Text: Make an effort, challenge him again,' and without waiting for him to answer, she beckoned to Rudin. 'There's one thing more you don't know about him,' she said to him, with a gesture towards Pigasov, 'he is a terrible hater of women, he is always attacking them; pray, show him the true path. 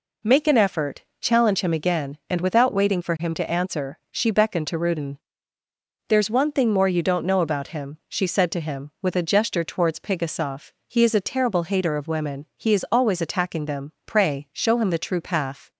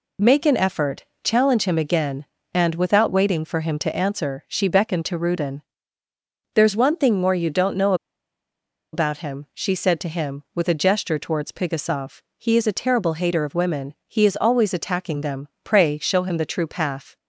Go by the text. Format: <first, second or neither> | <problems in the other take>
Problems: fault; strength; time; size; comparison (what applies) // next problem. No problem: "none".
first | pauses between "know" and "about"; at 7.9 s; 0.98 s long